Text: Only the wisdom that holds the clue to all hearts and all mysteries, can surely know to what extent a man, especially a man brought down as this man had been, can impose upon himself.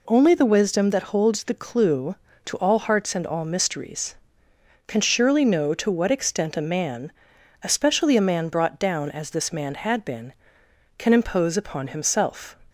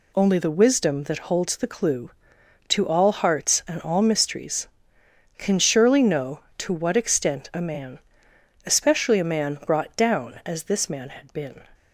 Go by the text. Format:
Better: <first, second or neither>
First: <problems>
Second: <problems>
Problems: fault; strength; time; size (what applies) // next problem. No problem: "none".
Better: first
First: none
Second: stops before "can impose upon himself"; at 11.7 s